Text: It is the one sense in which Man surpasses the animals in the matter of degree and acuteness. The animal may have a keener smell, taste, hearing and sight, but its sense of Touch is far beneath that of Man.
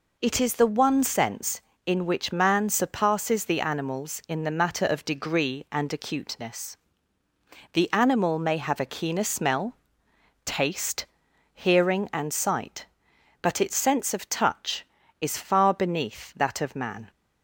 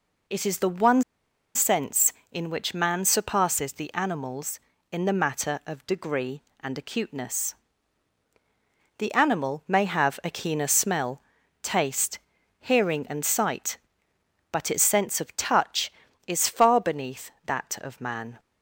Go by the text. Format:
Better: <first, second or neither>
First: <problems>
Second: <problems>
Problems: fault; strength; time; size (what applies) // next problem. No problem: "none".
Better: first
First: none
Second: pauses between "one" and "sense"; noticeable; at 1.0 s; 0.53 s long